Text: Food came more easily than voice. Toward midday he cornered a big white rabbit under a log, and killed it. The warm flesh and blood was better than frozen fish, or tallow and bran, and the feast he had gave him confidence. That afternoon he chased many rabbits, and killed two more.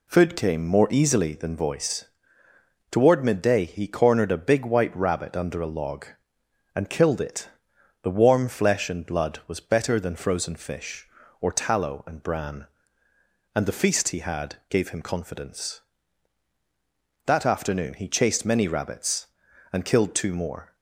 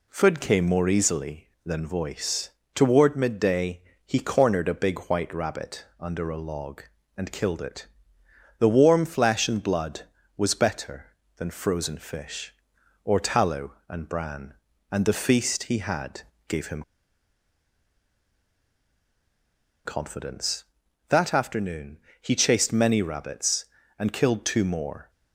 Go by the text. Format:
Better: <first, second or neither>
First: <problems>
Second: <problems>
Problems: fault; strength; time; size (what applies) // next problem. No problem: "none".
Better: first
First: pauses between "had" and "gave"; slight; at 14.5 s; 0.16 s long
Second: pauses between "midday" and "he"; slight; at 3.8 s; 0.24 s long // pauses between "had" and "gave"; slight; at 16.2 s; 0.26 s long // pauses between "him" and "confidence"; strong; at 16.8 s; 3.0 s long // pauses between "afternoon" and "he"; slight; at 21.9 s; 0.24 s long